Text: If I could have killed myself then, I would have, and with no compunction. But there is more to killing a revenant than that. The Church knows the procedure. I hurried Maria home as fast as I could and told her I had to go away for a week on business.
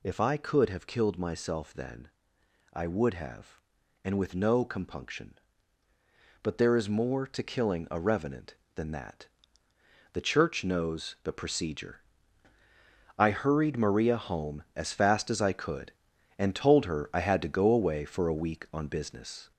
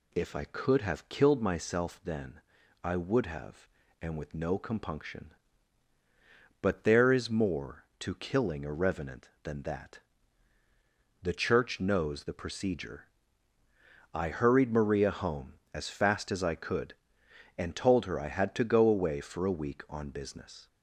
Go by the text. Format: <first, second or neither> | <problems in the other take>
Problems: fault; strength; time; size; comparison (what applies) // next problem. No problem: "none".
second | gets louder; noticeable; throughout; 4.5 dB